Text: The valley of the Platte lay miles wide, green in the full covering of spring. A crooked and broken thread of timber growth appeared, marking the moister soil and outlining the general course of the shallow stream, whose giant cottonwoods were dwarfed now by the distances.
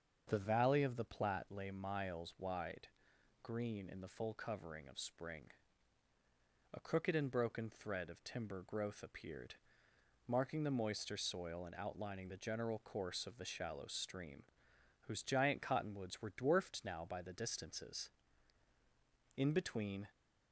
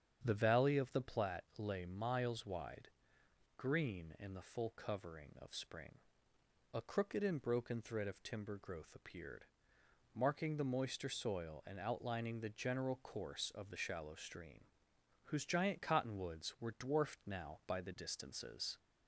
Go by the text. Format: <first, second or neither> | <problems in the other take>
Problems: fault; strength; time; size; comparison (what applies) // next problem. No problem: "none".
second | starts louder than the rest; until 1.2 s; 6.5 dB; strong in the second // goes on to say "In between"; noticeable; from 19.3 s on; 0.70 s long